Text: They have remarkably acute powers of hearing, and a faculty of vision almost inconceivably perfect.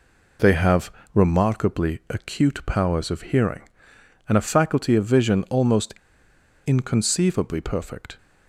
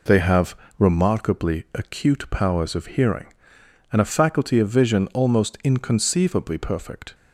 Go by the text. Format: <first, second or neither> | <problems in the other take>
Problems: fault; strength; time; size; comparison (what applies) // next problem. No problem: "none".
second | pauses between "have" and "remarkably"; slight; at 0.9 s; 0.22 s long; slight in the second // pauses between "almost" and "inconceivably"; noticeable; at 5.9 s; 0.74 s long